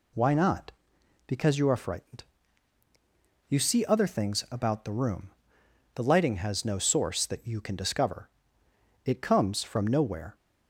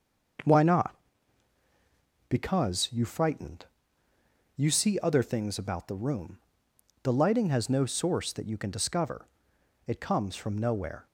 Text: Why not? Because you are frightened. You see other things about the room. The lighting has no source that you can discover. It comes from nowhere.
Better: first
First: none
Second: starts louder than the rest; until 2.7 s; 6 dB // skips "are"; at 3.0 s

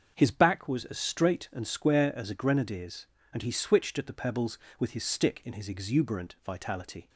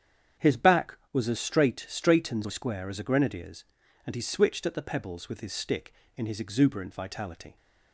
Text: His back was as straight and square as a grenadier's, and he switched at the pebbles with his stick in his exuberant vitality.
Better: first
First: starts louder than the rest; until 1.1 s; 6.5 dB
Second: starts louder than the rest; strong; until 1.5 s; 8.5 dB // says "straight" twice; at 1.8 s

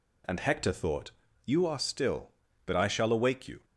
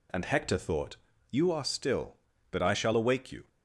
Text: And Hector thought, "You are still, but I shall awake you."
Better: neither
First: none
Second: none

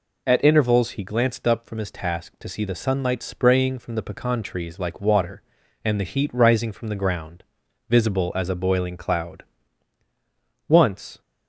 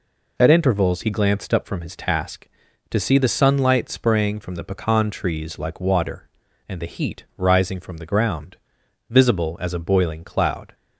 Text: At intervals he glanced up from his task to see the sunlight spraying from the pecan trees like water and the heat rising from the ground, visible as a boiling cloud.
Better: second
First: goes on to say "Once"; from 10.6 s on; 0.52 s long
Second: none

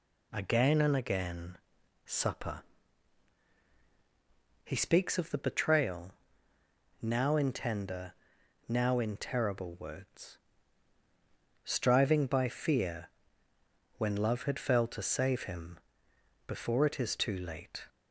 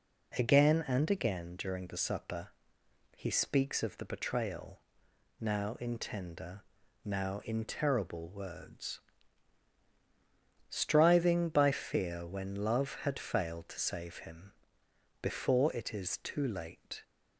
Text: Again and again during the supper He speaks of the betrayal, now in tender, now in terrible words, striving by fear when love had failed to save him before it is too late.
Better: second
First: skips "during the"; at 1.8 s // pauses between "supper" and "He"; strong; at 2.6 s; 2.0 s long // pauses between "fear" and "when"; noticeable; at 13.0 s; 0.88 s long // pauses between "him" and "before"; noticeable; at 15.7 s; 0.70 s long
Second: pauses between "supper" and "He"; noticeable; at 2.4 s; 0.66 s long // pauses between "him" and "before"; noticeable; at 14.5 s; 0.68 s long

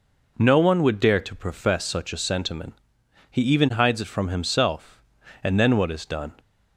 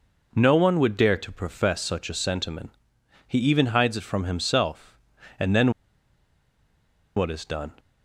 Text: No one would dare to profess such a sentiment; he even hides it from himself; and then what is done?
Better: first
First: none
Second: pauses between "then" and "what"; strong; at 5.7 s; 1.4 s long

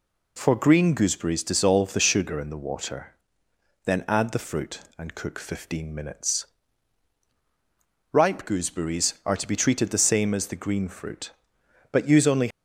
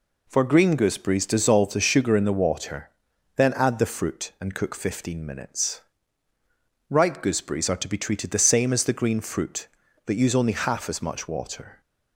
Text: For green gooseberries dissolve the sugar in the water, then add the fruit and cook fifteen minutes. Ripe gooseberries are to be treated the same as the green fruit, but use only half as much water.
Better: second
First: stops before "half as much water"; at 12.4 s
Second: none

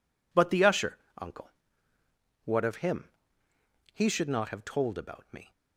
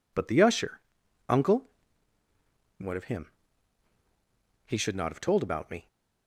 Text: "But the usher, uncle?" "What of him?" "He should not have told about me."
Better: neither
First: none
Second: none

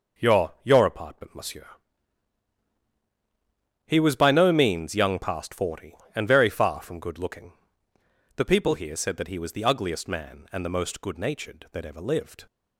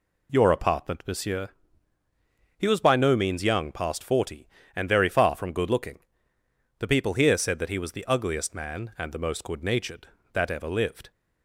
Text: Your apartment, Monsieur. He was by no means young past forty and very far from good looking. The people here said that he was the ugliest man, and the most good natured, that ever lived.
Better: second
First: says "Your" twice; at 0.6 s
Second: none

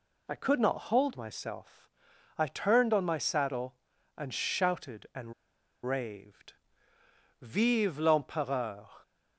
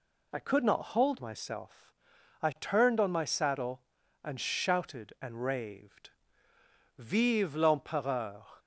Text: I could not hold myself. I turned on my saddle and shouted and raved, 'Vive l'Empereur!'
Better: second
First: pauses between "and" and "raved"; noticeable; at 5.3 s; 0.52 s long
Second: none

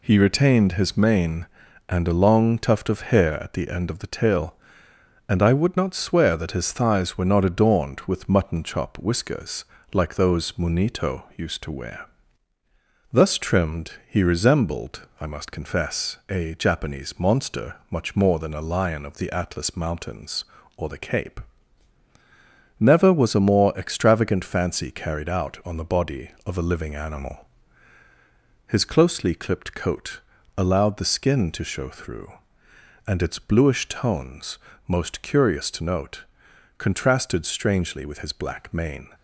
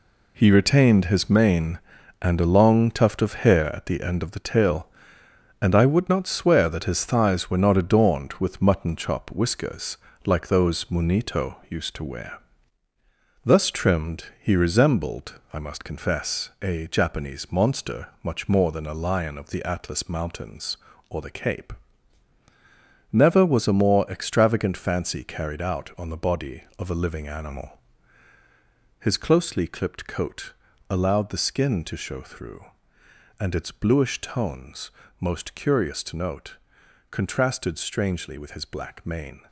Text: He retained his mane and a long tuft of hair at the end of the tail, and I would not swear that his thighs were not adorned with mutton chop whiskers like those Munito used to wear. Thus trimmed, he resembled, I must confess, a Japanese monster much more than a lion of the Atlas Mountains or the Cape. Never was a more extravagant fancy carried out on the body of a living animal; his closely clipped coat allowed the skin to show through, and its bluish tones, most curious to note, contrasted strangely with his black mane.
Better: first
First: pauses between "whiskers" and "like"; slight; at 9.6 s; 0.28 s long // pauses between "coat" and "allowed"; slight; at 30.2 s; 0.36 s long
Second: gets quieter; strong; throughout; 8.5 dB // pauses between "whiskers" and "like"; slight; at 9.9 s; 0.28 s long // pauses between "coat" and "allowed"; slight; at 30.5 s; 0.36 s long

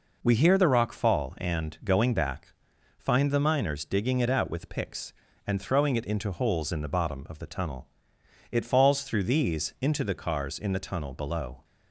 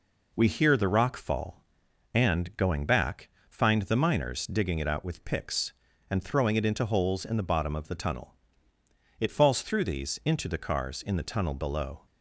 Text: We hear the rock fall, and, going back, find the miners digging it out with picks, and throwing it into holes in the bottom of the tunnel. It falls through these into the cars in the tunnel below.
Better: neither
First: none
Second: none

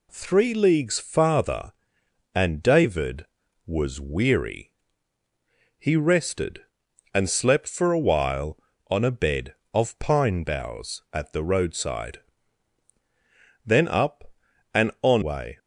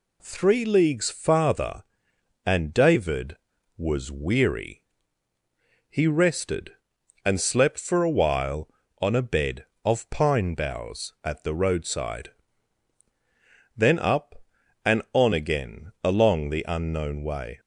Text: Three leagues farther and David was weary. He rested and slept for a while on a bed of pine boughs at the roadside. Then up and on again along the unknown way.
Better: second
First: skips "again along the unknown"; at 15.2 s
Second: none

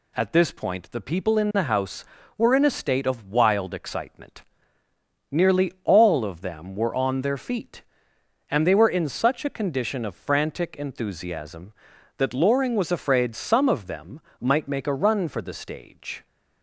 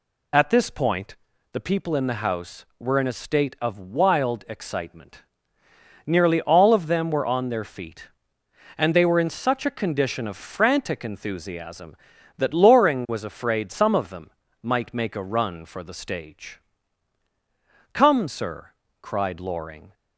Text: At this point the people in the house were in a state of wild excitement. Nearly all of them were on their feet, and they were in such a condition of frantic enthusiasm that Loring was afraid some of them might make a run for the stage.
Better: first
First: pauses between "them" and "might"; slight; at 14.2 s; 0.18 s long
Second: pauses between "point" and "the"; at 1.1 s; 0.38 s long // pauses between "them" and "might"; slight; at 14.2 s; 0.32 s long // goes on to say "Come sir cried Loring"; strong; from 17.9 s on; 2.0 s long

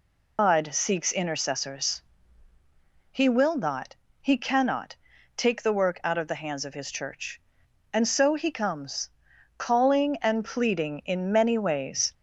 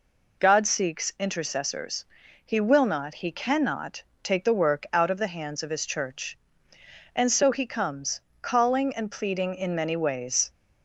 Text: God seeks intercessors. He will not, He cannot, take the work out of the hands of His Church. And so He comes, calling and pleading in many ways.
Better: second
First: loses the start of "God"; at 0.3 s; 135 ms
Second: none

